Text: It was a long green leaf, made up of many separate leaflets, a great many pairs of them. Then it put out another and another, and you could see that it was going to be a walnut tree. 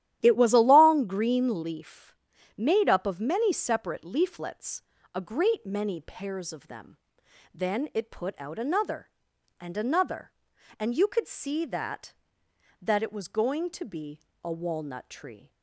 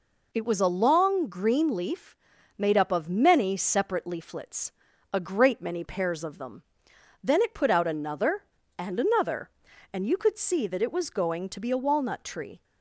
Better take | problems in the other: second | starts louder than the rest; strong; until 1.2 s; 12 dB // says "that" twice; at 12.8 s // pauses between "be" and "a"; slight; at 14.2 s; 0.21 s long

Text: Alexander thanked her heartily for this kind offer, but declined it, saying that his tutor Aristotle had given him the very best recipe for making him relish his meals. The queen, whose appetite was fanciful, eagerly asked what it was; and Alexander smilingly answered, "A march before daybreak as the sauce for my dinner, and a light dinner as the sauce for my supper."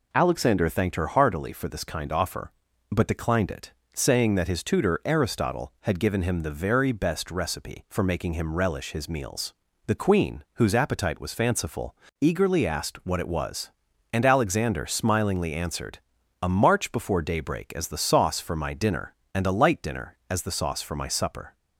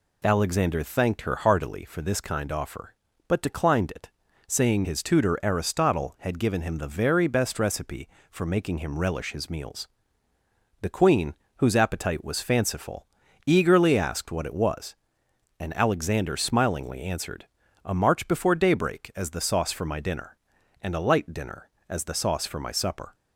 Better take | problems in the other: first | skips "that"; at 4.8 s

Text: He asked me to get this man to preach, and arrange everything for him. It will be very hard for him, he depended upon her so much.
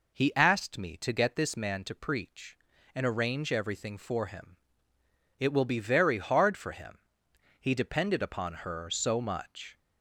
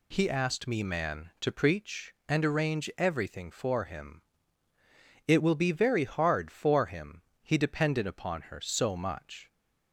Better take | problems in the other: first | skips "to get this"; at 0.8 s

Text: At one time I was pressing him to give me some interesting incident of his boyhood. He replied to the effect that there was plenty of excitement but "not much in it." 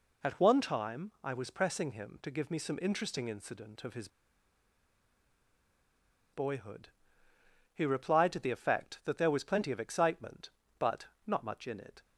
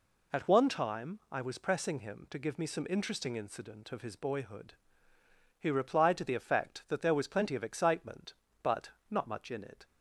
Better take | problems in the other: second | pauses between "his" and "boyhood"; strong; at 4.0 s; 2.2 s long // pauses between "but" and "not"; slight; at 11.0 s; 0.22 s long; slight in the second

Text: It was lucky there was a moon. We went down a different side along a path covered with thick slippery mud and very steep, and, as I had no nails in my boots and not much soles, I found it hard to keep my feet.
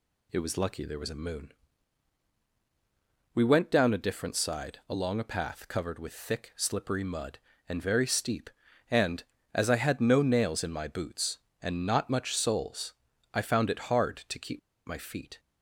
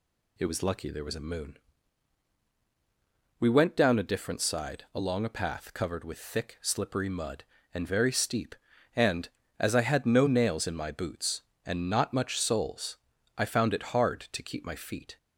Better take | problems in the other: second | pauses between "keep" and "my"; slight; at 14.5 s; 0.27 s long

